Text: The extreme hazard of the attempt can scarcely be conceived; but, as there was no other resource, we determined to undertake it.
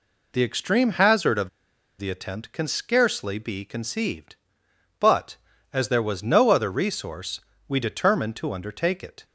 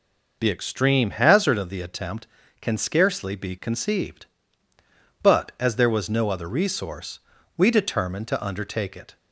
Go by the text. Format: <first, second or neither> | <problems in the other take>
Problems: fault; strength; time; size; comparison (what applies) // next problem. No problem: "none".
second | pauses between "of" and "the"; noticeable; at 1.4 s; 0.49 s long